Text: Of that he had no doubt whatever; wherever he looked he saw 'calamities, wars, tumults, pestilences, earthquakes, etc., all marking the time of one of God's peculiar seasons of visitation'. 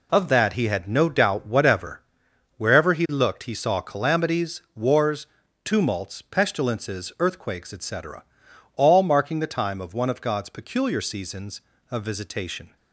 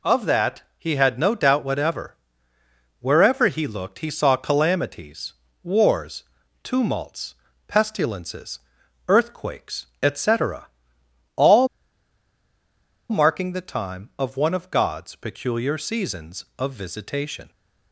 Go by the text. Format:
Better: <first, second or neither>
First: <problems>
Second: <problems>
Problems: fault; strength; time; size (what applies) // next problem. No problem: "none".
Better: first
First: none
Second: pauses between "that" and "he"; slight; at 0.6 s; 0.16 s long // pauses between "all" and "marking"; strong; at 11.6 s; 1.4 s long